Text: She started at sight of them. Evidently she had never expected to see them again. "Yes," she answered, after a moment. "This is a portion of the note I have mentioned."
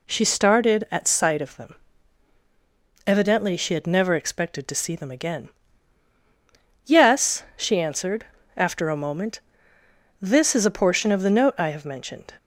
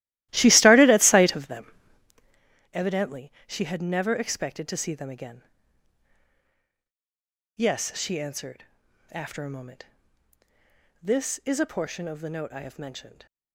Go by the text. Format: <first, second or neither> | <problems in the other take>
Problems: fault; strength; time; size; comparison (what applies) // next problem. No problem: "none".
first | starts louder than the rest; strong; until 2.2 s; 16.5 dB // pauses between "Evidently" and "she"; slight; at 3.3 s; 0.16 s long